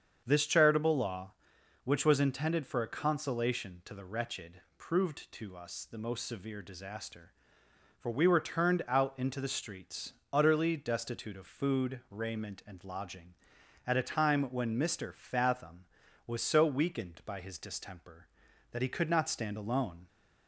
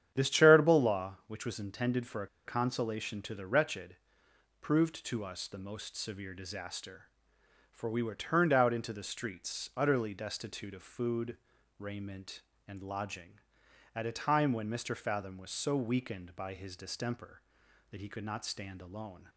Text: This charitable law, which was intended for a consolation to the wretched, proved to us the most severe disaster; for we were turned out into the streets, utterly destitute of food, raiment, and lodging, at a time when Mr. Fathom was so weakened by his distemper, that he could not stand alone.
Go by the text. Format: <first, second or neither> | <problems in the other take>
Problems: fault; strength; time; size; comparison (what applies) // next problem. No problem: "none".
first | starts louder than the rest; strong; until 1.1 s; 9.5 dB; strong in the first // pauses between "a" and "consolation"; slight; at 2.2 s; 0.18 s long